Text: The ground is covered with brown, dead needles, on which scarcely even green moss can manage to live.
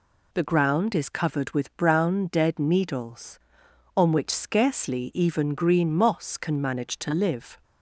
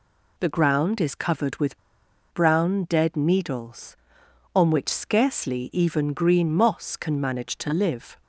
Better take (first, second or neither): first